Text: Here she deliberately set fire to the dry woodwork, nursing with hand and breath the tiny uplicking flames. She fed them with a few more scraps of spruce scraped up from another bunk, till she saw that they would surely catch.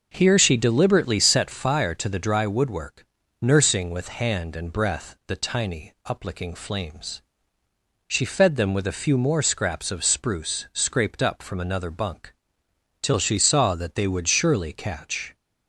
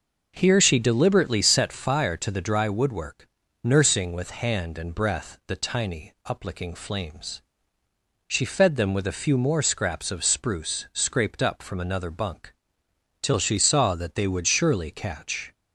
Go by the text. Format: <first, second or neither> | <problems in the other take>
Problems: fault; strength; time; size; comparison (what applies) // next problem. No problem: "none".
neither | none